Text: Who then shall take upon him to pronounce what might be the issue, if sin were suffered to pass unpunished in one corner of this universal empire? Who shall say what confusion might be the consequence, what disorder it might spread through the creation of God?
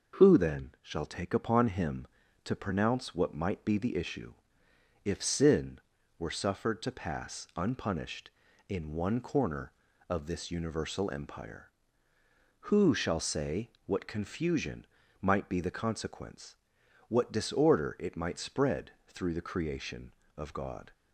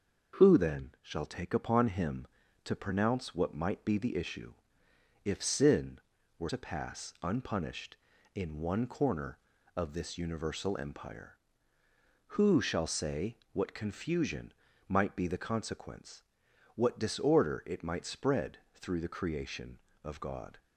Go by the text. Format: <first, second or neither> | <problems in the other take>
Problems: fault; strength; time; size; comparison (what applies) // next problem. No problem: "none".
first | starts louder than the rest; noticeable; until 1.4 s; 6 dB // skips "suffered"; at 6.4 s // pauses between "say" and "what"; slight; at 13.3 s; 0.16 s long; slight in the first // pauses between "confusion" and "might"; slight; at 14.5 s; 0.34 s long; slight in the first // pauses between "spread" and "through"; slight; at 18.5 s; 0.16 s long; slight in the first